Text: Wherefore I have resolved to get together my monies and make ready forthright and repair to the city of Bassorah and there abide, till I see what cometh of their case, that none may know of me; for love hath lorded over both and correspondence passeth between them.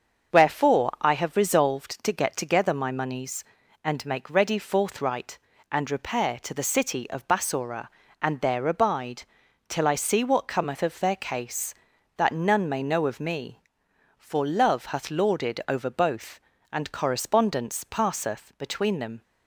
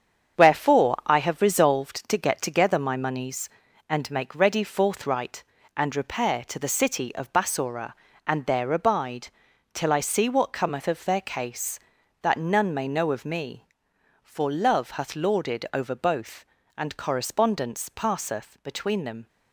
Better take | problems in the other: first | gets quieter; strong; throughout; 7.5 dB // starts louder than the rest; strong; until 1.4 s; 7.5 dB; also in the first

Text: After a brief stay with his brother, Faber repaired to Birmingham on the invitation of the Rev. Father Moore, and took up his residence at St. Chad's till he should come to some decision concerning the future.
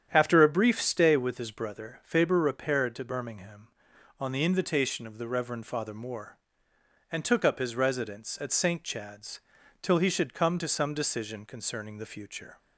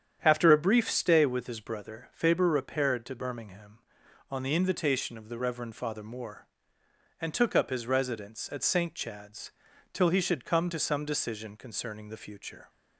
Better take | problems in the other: neither | starts louder than the rest; strong; the same in both // pauses between "Chad's" and "till"; the same in both

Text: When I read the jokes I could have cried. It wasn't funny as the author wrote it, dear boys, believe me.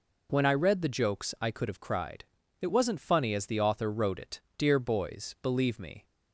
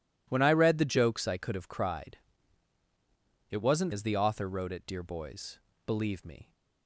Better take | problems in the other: first | skips "funny"; at 3.9 s

